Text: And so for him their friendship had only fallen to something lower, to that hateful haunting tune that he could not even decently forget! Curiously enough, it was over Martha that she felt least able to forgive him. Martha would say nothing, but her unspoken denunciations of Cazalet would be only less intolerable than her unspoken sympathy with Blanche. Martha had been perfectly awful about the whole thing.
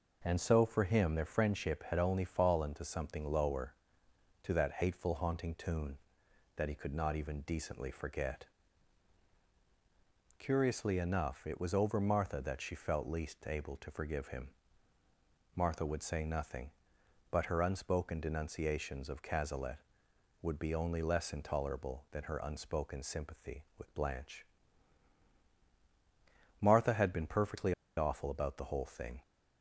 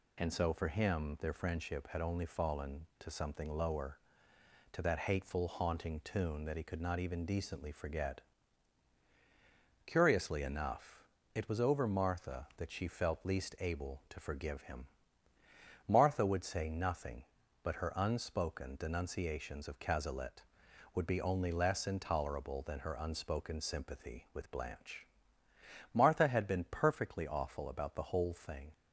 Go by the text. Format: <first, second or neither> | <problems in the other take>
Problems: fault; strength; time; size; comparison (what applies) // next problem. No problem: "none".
second | pauses between "perfectly" and "awful"; slight; at 27.7 s; 0.24 s long